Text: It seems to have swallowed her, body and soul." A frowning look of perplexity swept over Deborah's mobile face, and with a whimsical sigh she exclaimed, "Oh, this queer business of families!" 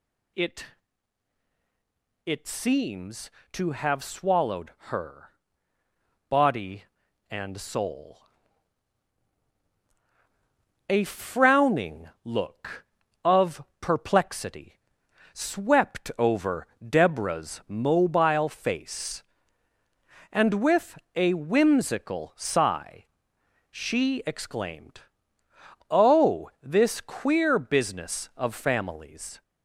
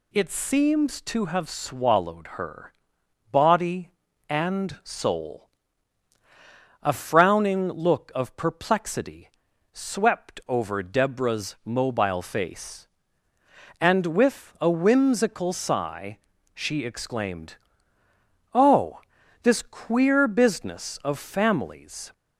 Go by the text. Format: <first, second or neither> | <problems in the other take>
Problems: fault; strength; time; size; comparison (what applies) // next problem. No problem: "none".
second | says "It" twice; at 2.2 s // pauses between "swallowed" and "her"; slight; at 4.6 s; 0.20 s long // pauses between "frowning" and "look"; slight; at 12.0 s; 0.16 s long // pauses between "of" and "perplexity"; slight; at 13.6 s; 0.20 s long // pauses between "perplexity" and "swept"; noticeable; at 14.7 s; 0.56 s long; also in the second // pauses between "over" and "Deborah's"; slight; at 16.6 s; 0.22 s long // pauses between "with" and "a"; slight; at 20.9 s; 0.16 s long // pauses between "sigh" and "she"; noticeable; at 23.0 s; 0.66 s long; slight in the second